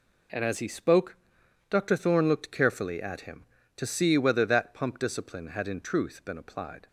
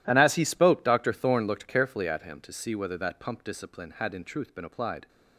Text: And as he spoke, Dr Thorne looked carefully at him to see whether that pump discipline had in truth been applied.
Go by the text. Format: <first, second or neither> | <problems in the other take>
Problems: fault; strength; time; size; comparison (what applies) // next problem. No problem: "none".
neither | none